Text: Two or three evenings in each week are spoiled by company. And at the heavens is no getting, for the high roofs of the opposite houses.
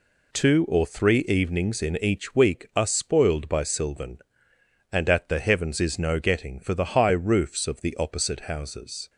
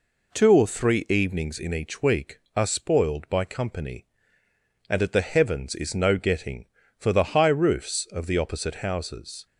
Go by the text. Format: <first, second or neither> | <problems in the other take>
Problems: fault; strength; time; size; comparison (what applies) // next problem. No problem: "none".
second | says "sylvan" for "company"; at 3.6 s